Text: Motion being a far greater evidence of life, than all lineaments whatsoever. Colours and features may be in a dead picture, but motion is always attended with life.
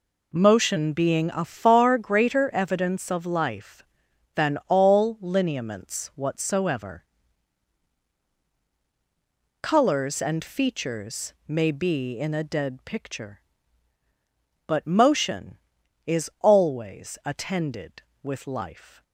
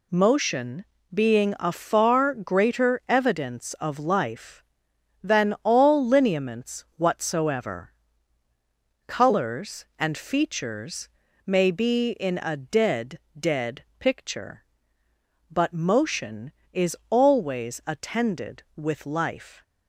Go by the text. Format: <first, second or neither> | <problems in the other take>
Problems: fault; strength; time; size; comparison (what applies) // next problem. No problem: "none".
first | pauses between "Motion" and "being"; slight; at 0.8 s; 0.28 s long // pauses between "features" and "may"; slight; at 11.0 s; 0.36 s long // says "dead" twice; at 13.3 s